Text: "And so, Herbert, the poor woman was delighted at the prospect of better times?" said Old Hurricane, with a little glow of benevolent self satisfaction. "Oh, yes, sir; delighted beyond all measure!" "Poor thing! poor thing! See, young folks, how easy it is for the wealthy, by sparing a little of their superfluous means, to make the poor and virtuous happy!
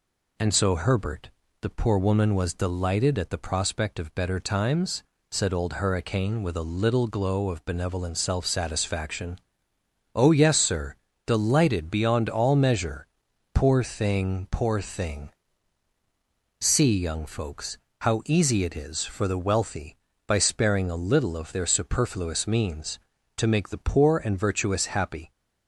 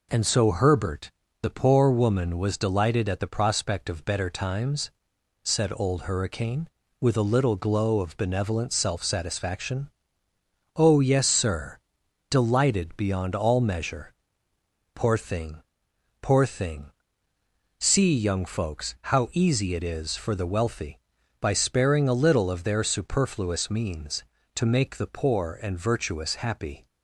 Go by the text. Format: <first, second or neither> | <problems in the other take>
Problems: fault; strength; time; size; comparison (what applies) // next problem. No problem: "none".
neither | none